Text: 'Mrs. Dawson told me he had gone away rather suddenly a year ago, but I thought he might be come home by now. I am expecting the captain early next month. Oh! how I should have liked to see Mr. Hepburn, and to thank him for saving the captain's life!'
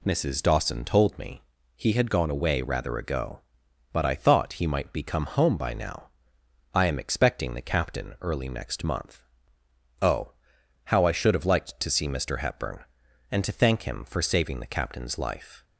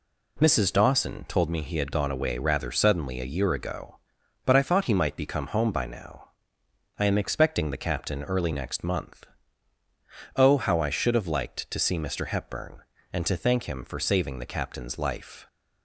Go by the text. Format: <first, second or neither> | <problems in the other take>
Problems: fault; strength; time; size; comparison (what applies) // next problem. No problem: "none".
second | pauses between "me" and "he"; slight; at 1.4 s; 0.34 s long // skips "suddenly a year"; at 2.9 s